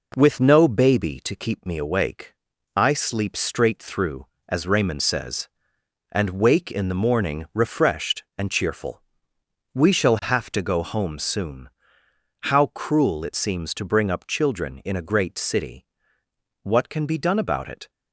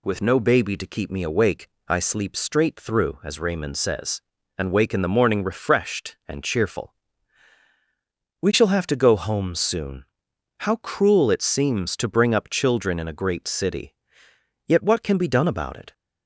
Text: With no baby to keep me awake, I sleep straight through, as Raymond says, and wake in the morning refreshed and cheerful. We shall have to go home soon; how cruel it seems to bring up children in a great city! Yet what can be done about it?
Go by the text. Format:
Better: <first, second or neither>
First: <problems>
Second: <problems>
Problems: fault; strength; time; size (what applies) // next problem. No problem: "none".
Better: second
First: skips "Yet"; at 16.2 s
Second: none